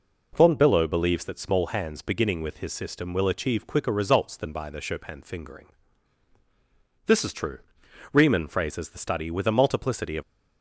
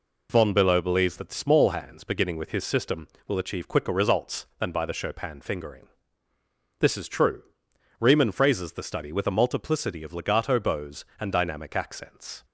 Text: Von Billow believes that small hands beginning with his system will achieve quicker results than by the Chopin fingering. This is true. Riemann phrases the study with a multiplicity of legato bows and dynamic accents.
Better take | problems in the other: second | stops before "legato bows and dynamic accents"; at 10.2 s

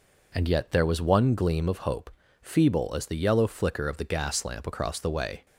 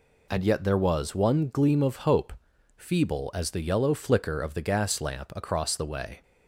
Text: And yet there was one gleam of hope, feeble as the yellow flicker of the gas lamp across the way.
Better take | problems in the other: neither | none

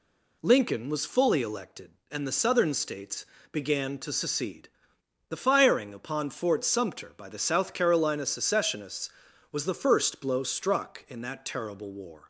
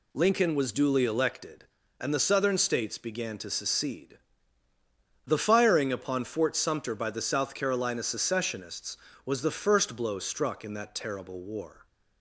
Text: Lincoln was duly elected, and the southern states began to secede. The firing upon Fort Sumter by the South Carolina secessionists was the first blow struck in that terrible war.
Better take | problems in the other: second | says "fully" for "duly"; at 1.0 s // pauses between "states" and "began"; slight; at 3.2 s; 0.26 s long

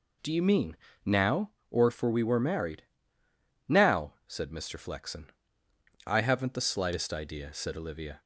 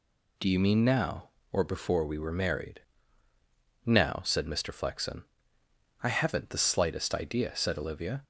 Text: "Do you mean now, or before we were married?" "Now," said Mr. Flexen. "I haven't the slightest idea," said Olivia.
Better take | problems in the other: second | pauses between "mean" and "now"; slight; at 0.7 s; 0.28 s long // says "for" for "before"; at 1.9 s

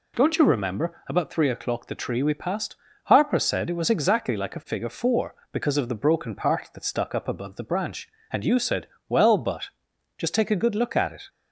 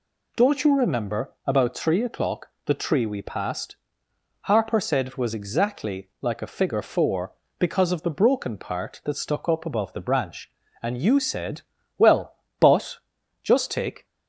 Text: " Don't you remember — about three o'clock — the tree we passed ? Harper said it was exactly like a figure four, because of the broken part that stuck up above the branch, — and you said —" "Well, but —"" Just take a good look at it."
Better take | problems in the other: first | stops before "a good look at it"; at 14.0 s

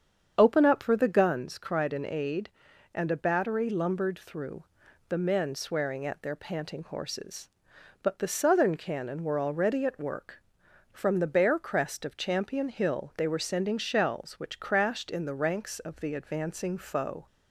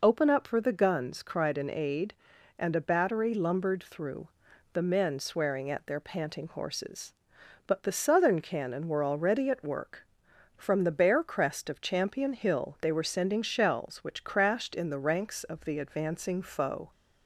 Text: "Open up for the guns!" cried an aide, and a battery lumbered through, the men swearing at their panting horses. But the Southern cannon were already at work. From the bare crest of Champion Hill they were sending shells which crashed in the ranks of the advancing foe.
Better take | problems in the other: second | starts louder than the rest; strong; until 1.4 s; 7.5 dB

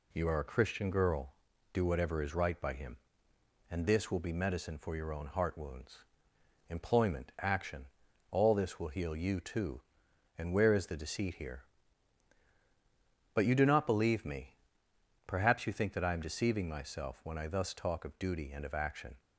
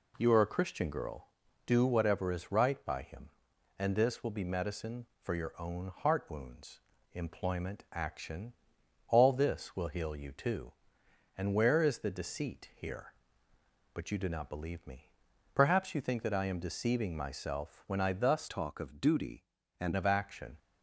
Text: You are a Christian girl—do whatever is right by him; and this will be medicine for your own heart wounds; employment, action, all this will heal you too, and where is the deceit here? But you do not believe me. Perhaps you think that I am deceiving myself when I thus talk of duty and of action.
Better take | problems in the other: first | changes voice from "talk" to "and"; from 18.4 to 19.9 s; 1.5 s long

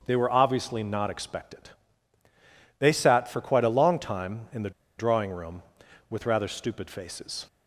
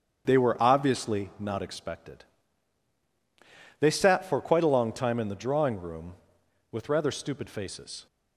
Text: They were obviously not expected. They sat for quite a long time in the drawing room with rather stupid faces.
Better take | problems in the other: second | starts louder than the rest; until 1.0 s; 6.5 dB; strong in the second // pauses between "the" and "drawing"; slight; at 4.6 s; 0.27 s long

